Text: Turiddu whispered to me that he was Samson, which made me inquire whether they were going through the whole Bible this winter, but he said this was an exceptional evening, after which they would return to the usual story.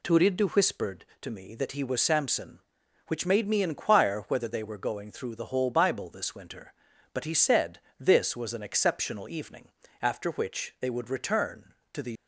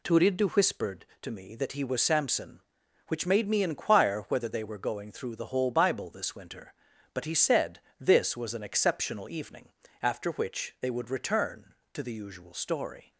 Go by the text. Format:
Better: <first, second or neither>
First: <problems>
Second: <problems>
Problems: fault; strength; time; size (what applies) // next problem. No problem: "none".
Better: second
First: pauses between "said" and "this"; slight; at 7.7 s; 0.20 s long // stops before "usual story"; at 12.1 s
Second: pauses between "said" and "this"; slight; at 7.7 s; 0.20 s long